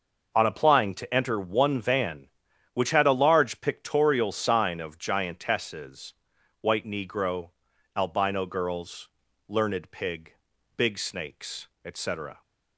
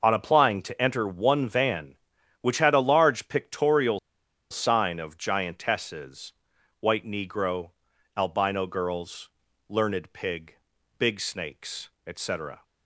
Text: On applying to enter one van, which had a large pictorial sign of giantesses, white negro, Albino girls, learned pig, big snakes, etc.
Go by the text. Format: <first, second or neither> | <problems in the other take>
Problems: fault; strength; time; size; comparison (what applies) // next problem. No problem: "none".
first | pauses between "pictorial" and "sign"; noticeable; at 3.9 s; 0.51 s long